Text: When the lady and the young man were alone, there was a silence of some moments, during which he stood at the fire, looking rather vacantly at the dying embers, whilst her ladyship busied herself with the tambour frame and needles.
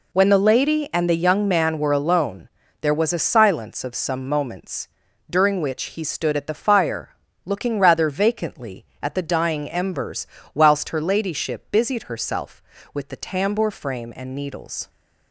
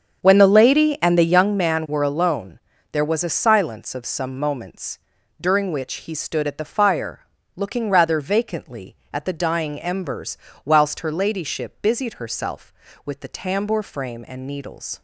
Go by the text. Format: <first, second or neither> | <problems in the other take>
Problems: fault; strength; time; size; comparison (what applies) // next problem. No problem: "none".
first | starts louder than the rest; strong; until 1.5 s; 7 dB